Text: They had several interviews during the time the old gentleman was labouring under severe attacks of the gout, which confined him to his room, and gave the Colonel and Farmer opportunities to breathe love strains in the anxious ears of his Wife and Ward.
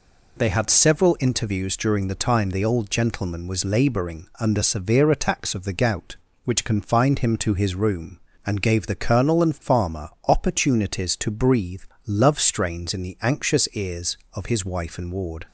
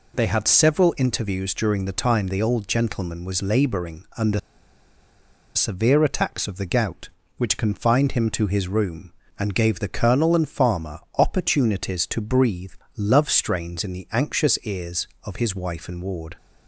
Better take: first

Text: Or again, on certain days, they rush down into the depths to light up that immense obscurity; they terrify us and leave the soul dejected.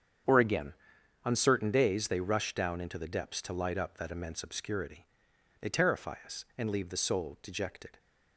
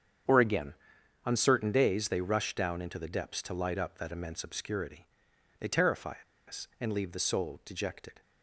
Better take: first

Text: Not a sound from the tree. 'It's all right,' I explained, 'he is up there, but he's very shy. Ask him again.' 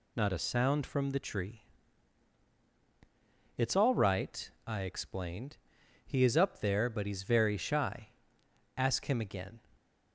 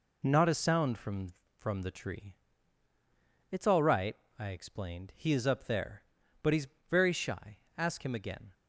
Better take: first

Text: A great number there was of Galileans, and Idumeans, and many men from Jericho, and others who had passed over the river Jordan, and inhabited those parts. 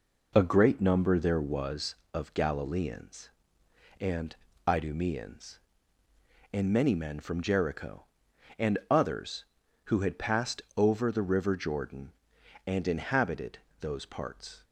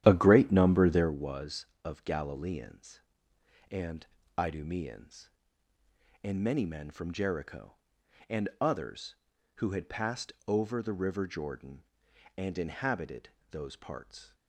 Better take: first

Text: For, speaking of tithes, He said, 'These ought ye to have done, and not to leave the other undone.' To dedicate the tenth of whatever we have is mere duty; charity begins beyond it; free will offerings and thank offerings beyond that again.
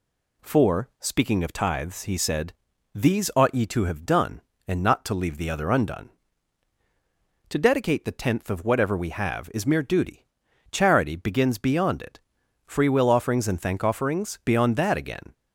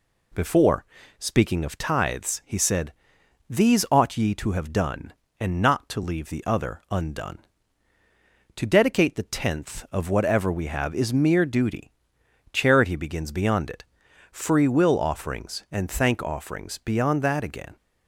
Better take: first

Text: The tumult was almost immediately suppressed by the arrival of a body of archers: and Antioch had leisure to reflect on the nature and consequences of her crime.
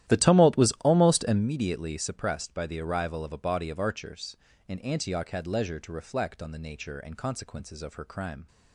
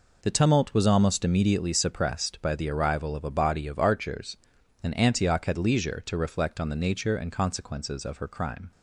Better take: second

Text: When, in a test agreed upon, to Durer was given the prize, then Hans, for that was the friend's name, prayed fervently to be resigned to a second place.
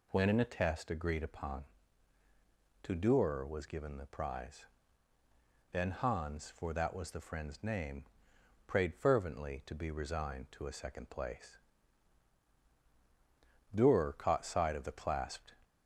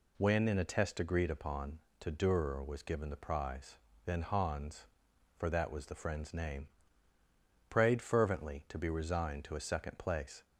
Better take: second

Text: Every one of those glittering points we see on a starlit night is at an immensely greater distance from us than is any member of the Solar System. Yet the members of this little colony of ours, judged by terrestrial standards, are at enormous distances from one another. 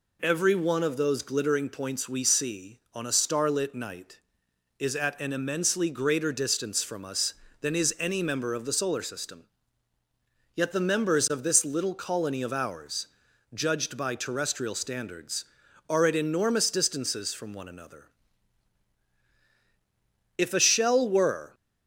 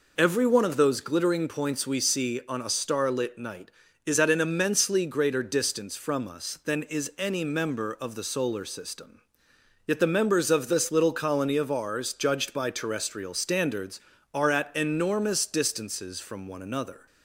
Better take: second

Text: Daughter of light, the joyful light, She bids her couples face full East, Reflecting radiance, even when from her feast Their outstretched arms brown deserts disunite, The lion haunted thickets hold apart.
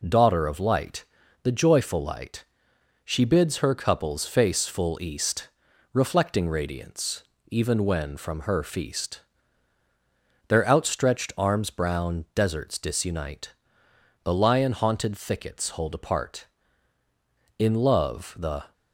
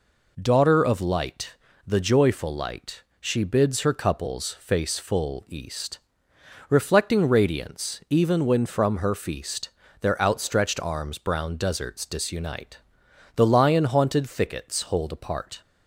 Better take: second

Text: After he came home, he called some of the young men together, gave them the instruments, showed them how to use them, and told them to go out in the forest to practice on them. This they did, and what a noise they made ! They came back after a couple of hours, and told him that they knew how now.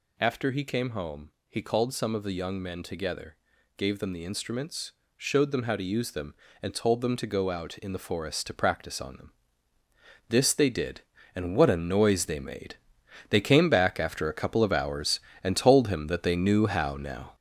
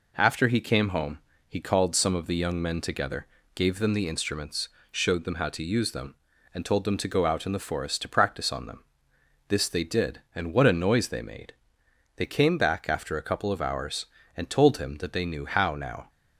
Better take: second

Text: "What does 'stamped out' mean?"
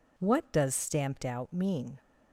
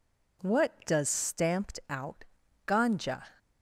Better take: first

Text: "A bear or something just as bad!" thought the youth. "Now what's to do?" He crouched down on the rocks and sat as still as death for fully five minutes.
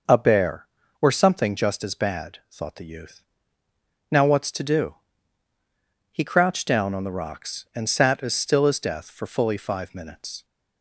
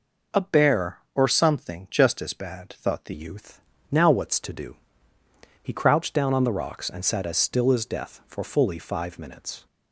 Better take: first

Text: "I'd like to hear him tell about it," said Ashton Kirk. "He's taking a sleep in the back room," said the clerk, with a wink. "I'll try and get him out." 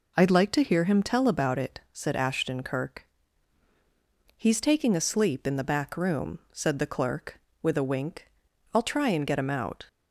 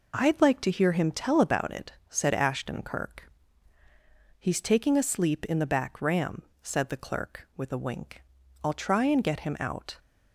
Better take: first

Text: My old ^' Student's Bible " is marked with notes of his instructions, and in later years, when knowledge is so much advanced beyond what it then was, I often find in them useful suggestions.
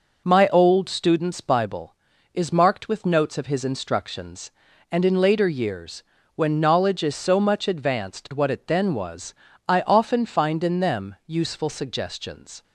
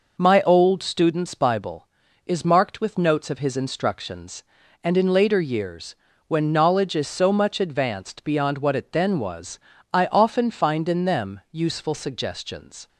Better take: second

